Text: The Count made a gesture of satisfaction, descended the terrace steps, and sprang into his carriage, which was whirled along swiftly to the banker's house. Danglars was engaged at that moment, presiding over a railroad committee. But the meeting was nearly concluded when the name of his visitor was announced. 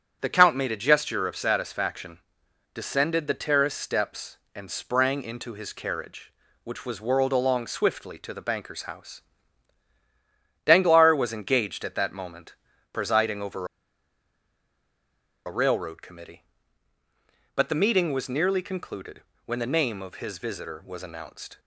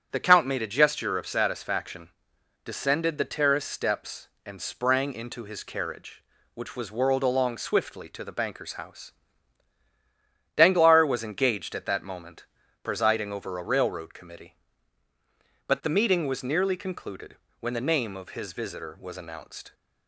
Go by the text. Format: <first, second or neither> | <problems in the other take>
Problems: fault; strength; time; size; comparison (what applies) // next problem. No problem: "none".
second | starts louder than the rest; strong; until 1.2 s; 8 dB; strong in the second // pauses between "over" and "a"; strong; at 13.6 s; 1.7 s long // pauses between "concluded" and "when"; slight; at 19.2 s; 0.22 s long; slight in the second